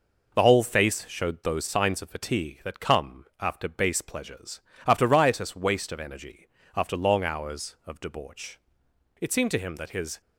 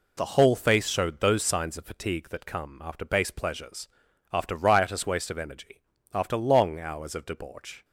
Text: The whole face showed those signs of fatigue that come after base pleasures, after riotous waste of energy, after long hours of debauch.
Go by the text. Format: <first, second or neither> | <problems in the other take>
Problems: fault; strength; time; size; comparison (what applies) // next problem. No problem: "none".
second | pauses between "come" and "after"; slight; at 3.2 s; 0.16 s long // goes on to say "It seemed to him that his"; noticeable; from 9.2 s on; 1.0 s long